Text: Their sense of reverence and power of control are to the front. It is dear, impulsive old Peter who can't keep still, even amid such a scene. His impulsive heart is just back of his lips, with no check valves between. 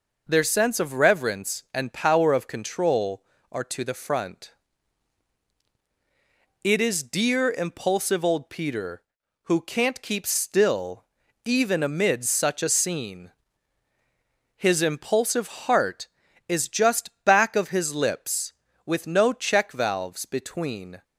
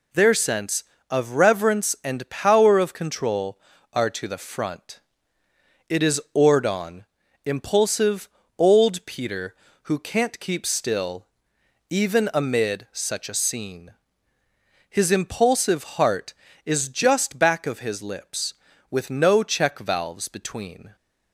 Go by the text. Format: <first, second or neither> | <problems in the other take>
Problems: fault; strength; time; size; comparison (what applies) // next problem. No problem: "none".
first | says "ordon" for "dear"; at 6.3 s // pauses between "impulsive" and "old"; slight; at 8.2 s; 0.30 s long